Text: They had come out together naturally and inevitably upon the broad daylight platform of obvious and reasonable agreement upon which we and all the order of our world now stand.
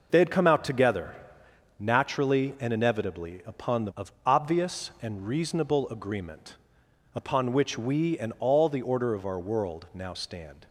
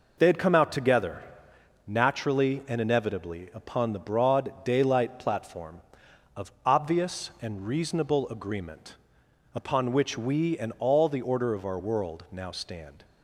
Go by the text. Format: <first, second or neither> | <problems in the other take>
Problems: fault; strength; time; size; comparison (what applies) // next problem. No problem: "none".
second | pauses between "together" and "naturally"; noticeable; at 1.1 s; 0.64 s long; noticeable in the second // skips "broad daylight platform"; at 3.9 s // pauses between "agreement" and "upon"; noticeable; at 6.5 s; 0.60 s long; noticeable in the second